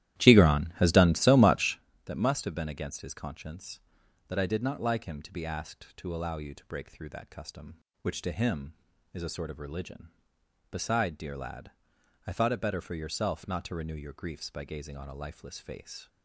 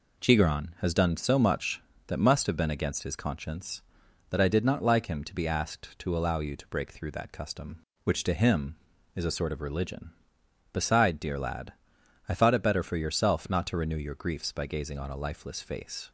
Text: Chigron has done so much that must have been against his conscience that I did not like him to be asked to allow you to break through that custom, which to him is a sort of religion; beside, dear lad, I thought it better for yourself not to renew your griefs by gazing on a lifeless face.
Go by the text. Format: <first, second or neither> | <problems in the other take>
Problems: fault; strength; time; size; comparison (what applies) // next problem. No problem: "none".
second | starts louder than the rest; strong; until 1.8 s; 13.5 dB